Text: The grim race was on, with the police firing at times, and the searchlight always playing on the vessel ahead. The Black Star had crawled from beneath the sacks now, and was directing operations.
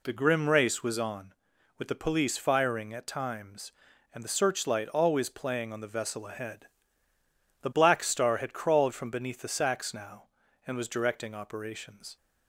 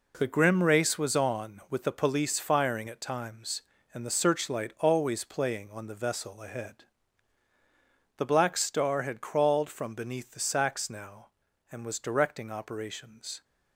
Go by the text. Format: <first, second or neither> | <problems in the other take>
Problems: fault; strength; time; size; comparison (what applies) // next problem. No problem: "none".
first | gets quieter; strong; throughout; 9 dB